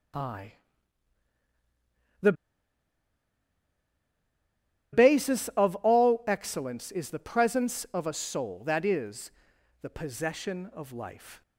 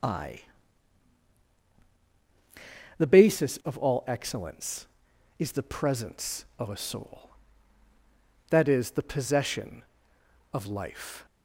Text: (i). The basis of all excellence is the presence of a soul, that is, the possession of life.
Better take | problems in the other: second | starts louder than the rest; strong; until 5.4 s; 9 dB; also in the second // pauses between "The" and "basis"; strong; at 2.3 s; 2.5 s long

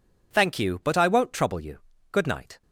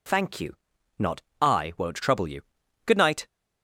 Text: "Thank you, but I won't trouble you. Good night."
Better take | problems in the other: first | says "not" for "but"; at 0.9 s

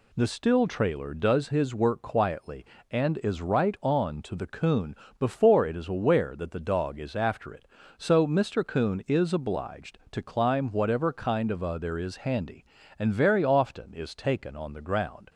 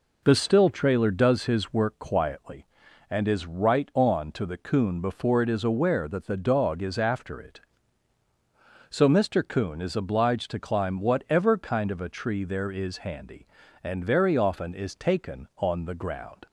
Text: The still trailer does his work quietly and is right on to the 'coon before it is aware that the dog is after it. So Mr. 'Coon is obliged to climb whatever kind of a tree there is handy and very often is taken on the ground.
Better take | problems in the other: second | pauses between "coon" and "before"; slight; at 4.9 s; 0.24 s long // skips "tree"; at 11.7 s

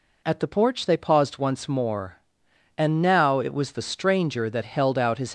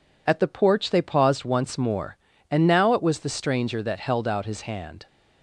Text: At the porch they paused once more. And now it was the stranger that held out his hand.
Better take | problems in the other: second | stops before "hand"; at 5.2 s

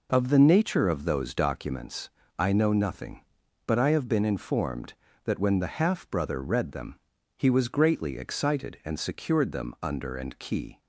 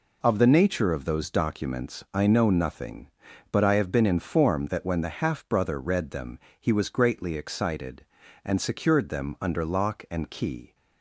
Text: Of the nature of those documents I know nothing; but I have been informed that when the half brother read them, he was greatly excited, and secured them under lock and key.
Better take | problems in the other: second | pauses between "documents" and "I"; slight; at 2.0 s; 0.28 s long // skips "lock"; at 10.1 s

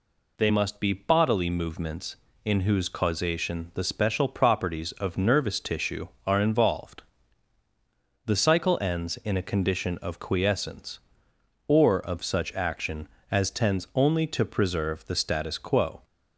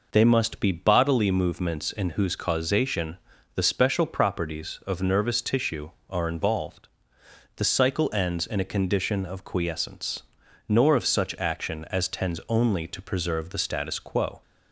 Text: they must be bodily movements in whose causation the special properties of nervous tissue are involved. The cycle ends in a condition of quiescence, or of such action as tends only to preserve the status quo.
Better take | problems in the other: first | pauses between "causation" and "the"; at 3.1 s; 0.38 s long // says "nor" for "or"; at 10.6 s

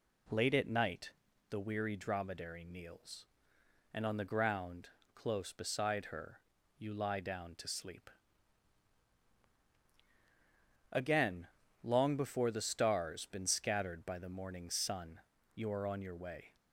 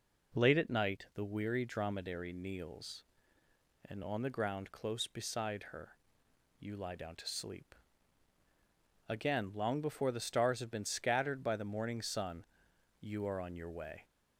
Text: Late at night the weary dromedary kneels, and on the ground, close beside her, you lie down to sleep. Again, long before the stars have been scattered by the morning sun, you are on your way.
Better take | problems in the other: second | pauses between "night" and "the"; at 1.1 s; 0.40 s long // skips "have"; at 13.2 s

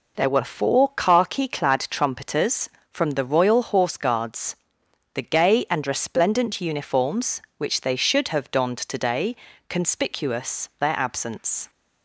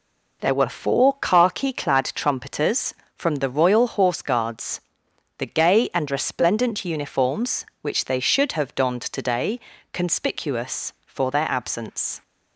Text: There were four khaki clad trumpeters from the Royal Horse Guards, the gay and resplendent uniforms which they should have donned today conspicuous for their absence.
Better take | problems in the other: second | pauses between "today" and "conspicuous"; slight; at 9.3 s; 0.32 s long; slight in the second // skips "for"; at 10.7 s

